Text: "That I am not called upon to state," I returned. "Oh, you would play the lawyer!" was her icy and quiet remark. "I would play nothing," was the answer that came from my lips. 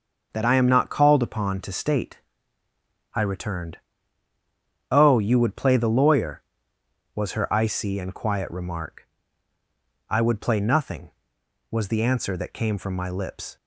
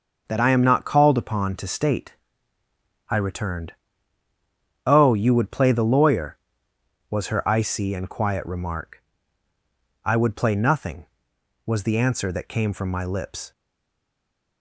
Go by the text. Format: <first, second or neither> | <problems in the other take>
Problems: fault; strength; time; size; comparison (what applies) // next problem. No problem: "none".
first | starts louder than the rest; noticeable; until 1.2 s; 6 dB; noticeable in the first // stays silent after the last word; from 13.5 s on; 1.1 s long